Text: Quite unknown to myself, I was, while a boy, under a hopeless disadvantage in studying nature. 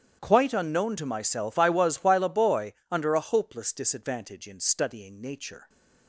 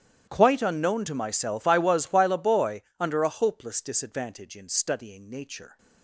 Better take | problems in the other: first | gets quieter; strong; throughout; 21.5 dB // starts louder than the rest; strong; until 1.3 s; 12 dB; strong in the first

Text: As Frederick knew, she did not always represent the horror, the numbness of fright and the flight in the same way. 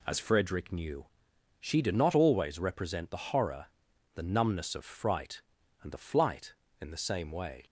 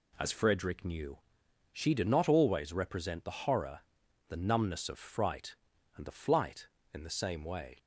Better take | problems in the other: neither | none

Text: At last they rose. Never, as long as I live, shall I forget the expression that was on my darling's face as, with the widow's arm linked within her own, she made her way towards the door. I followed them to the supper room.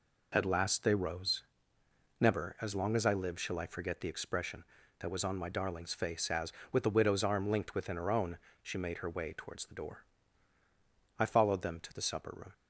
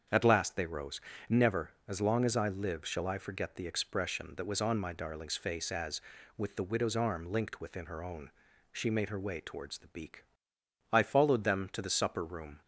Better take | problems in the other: first | starts louder than the rest; strong; until 1.3 s; 7 dB // says "beak" for "door"; at 9.8 s

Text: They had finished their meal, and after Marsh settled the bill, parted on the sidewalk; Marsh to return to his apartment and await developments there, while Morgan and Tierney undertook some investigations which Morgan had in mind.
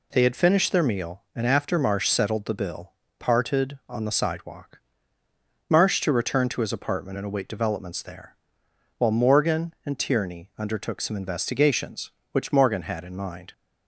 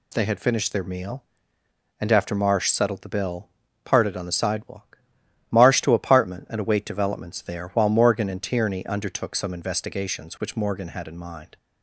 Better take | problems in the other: first | skips "return to his"; at 5.9 s

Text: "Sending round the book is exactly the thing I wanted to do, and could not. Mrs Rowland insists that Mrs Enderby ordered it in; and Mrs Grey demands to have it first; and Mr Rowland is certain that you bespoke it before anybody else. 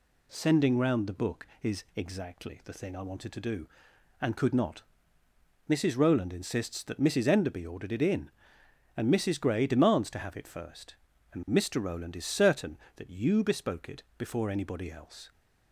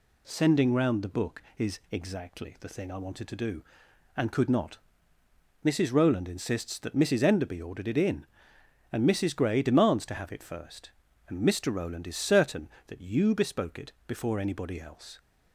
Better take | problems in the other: neither | pauses between "it" and "before"; slight; the same in both

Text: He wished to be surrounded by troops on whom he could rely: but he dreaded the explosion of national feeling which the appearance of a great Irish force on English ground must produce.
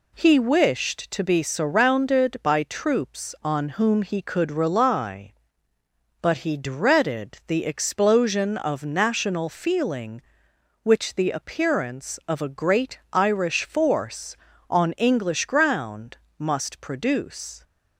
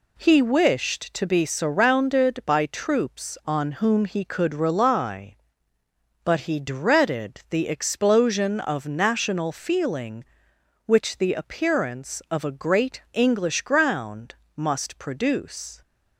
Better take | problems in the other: first | skips "Irish force on"; at 13.0 s // pauses between "ground" and "must"; slight; at 14.3 s; 0.20 s long; slight in the first

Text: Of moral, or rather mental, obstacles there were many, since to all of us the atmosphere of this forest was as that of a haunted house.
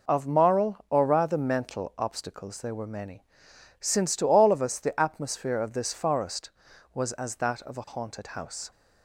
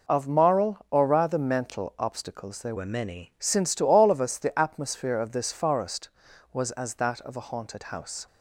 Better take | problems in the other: first | changes voice from "were" to "many"; from 2.7 to 3.3 s; 0.6 s long

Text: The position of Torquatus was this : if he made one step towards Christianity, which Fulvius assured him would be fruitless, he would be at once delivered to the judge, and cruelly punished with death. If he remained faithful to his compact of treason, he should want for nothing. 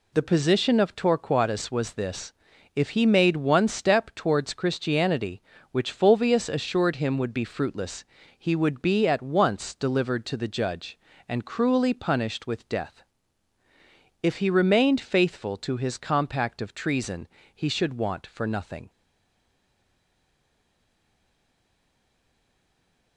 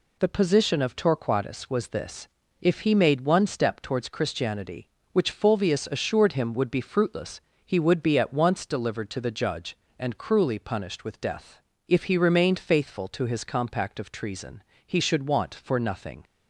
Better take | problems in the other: second | stays silent after the last word; strong; from 18.8 s on; 4.3 s long

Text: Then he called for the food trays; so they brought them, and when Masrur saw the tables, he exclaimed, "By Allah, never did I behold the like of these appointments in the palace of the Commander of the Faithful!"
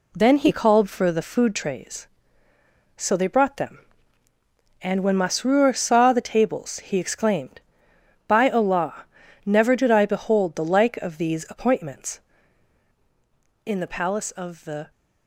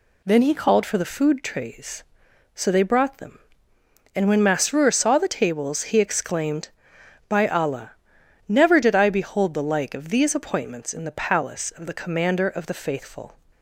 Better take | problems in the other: second | stops before "Commander of the Faithful"; at 14.9 s

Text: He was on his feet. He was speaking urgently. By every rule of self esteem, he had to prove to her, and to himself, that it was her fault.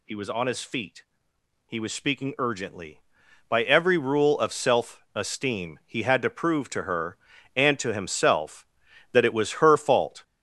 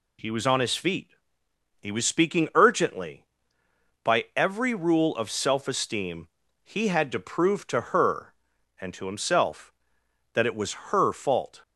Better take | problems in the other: second | gets louder; noticeable; throughout; 6 dB

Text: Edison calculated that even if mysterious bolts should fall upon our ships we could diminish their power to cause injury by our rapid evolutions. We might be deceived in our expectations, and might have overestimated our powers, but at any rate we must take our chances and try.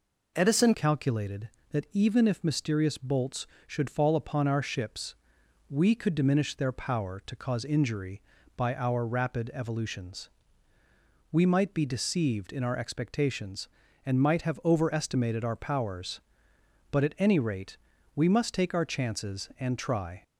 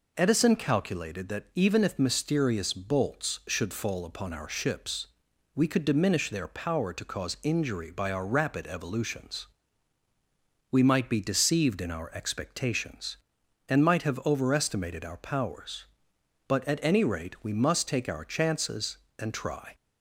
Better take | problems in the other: second | changes voice at "calculated"; from 0.7 s on; 19.5 s long // pauses between "ships" and "we"; noticeable; at 5.1 s; 0.54 s long; noticeable in the second // pauses between "rate" and "we"; at 17.7 s; 0.38 s long

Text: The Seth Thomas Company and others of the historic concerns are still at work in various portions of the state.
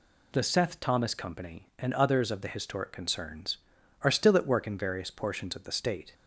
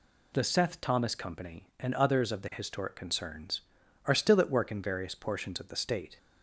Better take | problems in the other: neither | none

